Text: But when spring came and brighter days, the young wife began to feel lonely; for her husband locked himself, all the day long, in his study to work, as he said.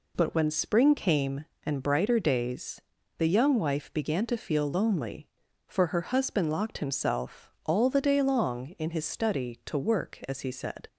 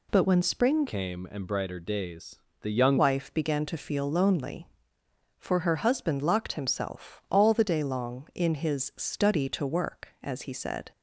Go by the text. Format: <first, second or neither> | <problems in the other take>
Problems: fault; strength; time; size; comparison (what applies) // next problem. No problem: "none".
first | changes voice from "came" to "young"; from 0.8 to 2.9 s; 2.1 s long